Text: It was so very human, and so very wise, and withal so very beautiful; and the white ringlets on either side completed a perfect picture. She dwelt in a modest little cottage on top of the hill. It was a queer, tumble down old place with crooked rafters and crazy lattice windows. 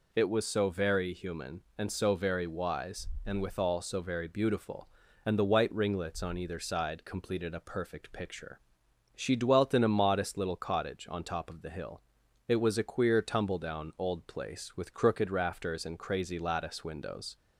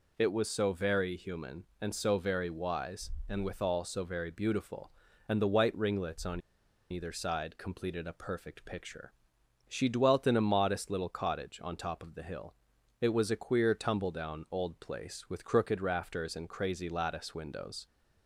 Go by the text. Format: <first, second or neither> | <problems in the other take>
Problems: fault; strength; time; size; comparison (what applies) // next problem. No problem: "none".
first | pauses between "on" and "either"; noticeable; at 6.3 s; 0.51 s long